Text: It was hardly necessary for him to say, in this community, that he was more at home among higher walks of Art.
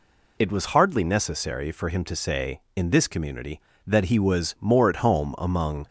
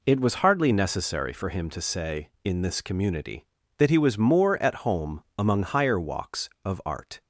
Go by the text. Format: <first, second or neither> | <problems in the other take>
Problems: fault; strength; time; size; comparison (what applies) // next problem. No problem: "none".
second | stops before "higher walks of Art"; at 5.8 s